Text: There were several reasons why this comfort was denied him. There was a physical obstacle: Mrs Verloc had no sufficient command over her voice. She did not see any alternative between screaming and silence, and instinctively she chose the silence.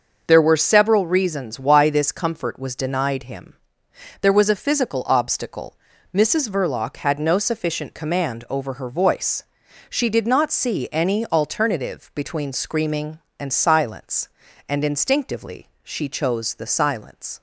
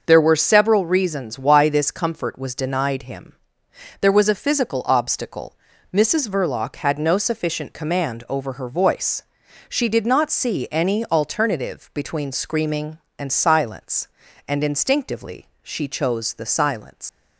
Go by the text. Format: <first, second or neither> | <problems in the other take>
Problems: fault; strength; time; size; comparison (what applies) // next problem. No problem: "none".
first | starts louder than the rest; noticeable; until 1.0 s; 6 dB; noticeable in the first // pauses between "instinctively" and "she"; slight; at 15.4 s; 0.16 s long; slight in the first // leaves "silence" unfinished; at 17.0 s; 105 ms